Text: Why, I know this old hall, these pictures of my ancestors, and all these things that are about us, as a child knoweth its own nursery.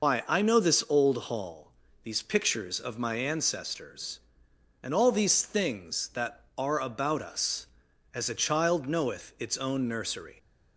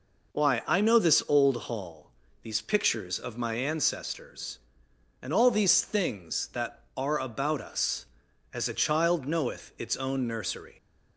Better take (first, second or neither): second